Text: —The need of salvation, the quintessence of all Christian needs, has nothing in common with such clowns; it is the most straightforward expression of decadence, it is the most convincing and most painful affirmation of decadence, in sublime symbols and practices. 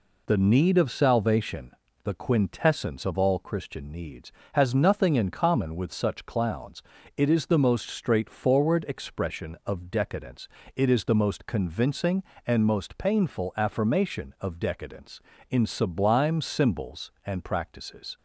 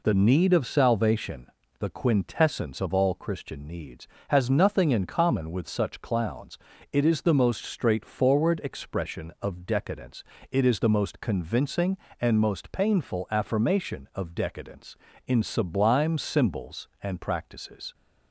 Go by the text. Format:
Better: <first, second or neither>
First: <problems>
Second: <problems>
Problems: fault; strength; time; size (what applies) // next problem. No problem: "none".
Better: neither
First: none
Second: none